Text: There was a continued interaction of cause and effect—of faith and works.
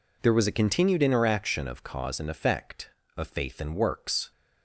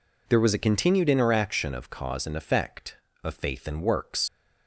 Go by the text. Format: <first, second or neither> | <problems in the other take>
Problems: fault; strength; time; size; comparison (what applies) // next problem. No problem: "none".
first | leaves "works" unfinished; at 4.2 s; 100 ms